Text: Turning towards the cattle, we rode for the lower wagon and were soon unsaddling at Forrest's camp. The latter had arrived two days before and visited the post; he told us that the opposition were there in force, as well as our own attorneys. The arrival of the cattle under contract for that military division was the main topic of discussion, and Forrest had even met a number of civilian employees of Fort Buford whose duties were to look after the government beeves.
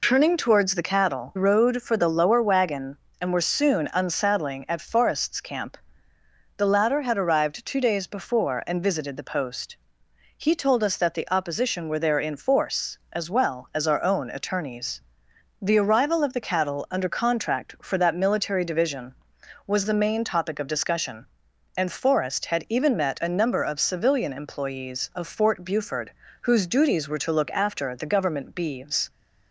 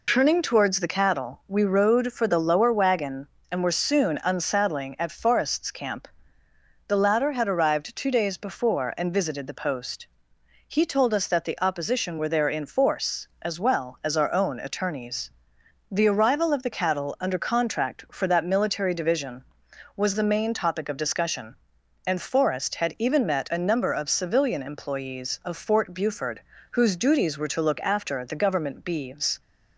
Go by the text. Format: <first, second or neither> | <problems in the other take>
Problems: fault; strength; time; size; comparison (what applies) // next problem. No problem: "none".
second | skips "we"; at 1.3 s // pauses between "Buford" and "whose"; slight; at 26.1 s; 0.30 s long; slight in the second